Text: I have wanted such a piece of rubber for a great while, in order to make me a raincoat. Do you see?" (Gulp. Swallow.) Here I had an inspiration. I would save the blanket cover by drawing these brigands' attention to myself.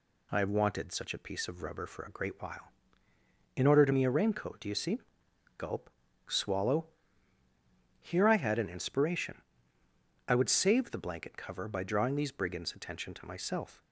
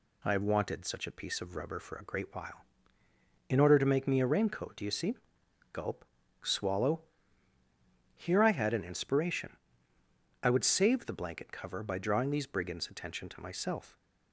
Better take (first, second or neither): second